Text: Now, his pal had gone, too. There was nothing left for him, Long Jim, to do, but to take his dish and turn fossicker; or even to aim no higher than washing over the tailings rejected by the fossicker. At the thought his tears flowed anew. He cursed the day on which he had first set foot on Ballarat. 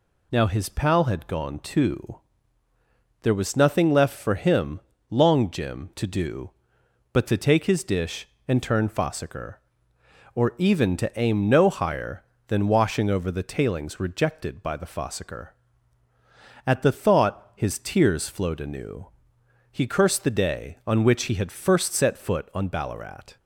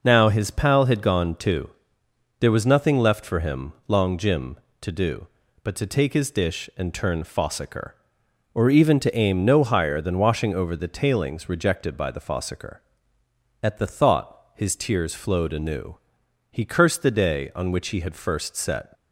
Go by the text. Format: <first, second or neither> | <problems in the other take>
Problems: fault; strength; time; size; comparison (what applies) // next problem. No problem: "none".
first | stops before "foot on Ballarat"; at 18.9 s